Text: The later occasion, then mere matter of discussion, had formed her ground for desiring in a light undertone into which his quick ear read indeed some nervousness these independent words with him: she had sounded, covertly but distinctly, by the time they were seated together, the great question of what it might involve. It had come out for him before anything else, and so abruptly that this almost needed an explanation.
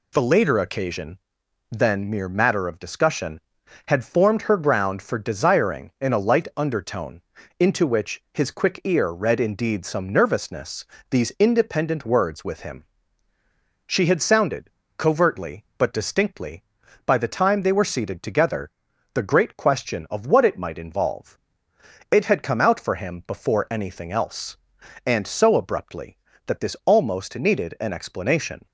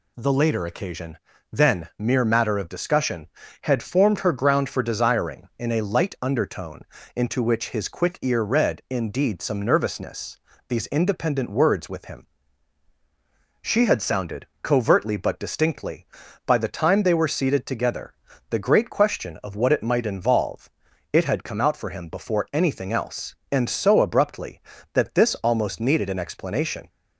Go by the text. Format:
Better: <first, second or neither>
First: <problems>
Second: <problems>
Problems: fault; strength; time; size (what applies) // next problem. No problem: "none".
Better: neither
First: pauses between "undertone" and "into"; slight; at 7.2 s; 0.36 s long // pauses between "nervousness" and "these"; slight; at 10.8 s; 0.24 s long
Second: pauses between "undertone" and "into"; slight; at 6.8 s; 0.34 s long // pauses between "nervousness" and "these"; slight; at 10.3 s; 0.32 s long